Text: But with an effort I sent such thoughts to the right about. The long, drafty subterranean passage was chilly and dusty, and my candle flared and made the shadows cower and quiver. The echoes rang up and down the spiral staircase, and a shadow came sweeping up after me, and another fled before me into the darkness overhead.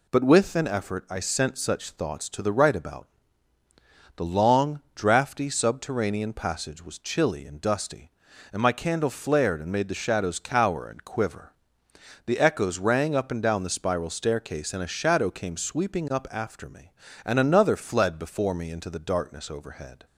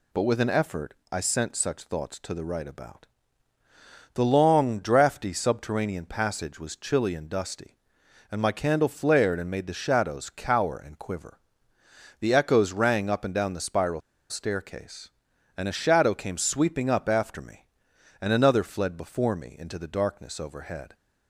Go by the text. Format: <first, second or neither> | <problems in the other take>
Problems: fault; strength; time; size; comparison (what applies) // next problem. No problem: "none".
first | pauses between "effort" and "I"; slight; at 0.9 s; 0.16 s long // pauses between "spiral" and "staircase"; slight; at 14.0 s; 0.29 s long